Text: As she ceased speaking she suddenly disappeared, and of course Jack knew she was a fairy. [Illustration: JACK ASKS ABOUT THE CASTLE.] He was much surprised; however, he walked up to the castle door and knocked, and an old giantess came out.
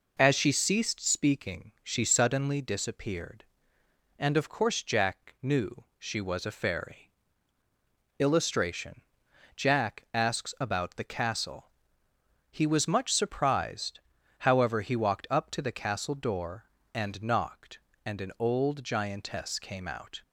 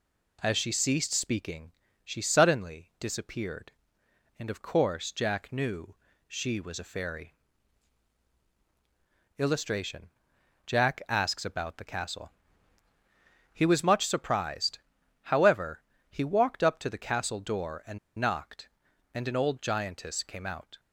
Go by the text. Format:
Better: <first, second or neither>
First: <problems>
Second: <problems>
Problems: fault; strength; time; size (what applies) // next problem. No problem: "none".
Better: first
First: pauses between "knew" and "she"; slight; at 5.8 s; 0.16 s long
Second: pauses between "speaking" and "she"; slight; at 1.7 s; 0.32 s long // pauses between "knew" and "she"; slight; at 5.9 s; 0.32 s long // pauses between "and" and "knocked"; slight; at 17.9 s; 0.20 s long